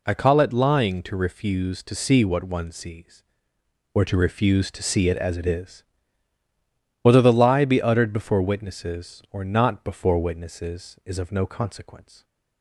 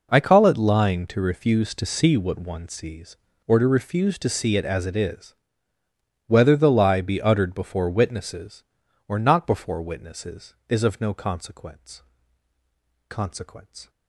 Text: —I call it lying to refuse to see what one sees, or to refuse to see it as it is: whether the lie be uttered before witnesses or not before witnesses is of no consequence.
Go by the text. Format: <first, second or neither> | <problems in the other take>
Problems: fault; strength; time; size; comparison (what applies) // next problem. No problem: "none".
first | says "consequence" twice; at 13.0 s